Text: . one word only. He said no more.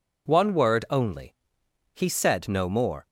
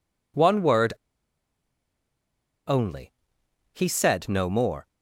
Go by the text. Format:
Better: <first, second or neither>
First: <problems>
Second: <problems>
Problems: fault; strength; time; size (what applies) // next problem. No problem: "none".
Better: first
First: none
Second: pauses between "word" and "only"; strong; at 0.9 s; 1.7 s long